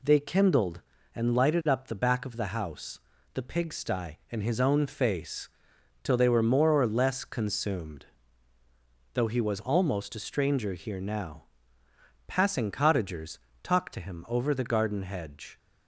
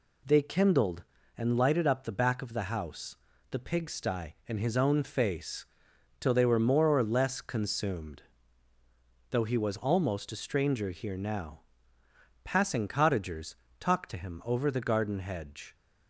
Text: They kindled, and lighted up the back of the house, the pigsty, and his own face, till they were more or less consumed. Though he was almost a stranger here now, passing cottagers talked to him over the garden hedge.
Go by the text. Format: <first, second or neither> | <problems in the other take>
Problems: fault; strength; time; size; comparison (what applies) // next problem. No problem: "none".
neither | pauses between "cottagers" and "talked"; slight; the same in both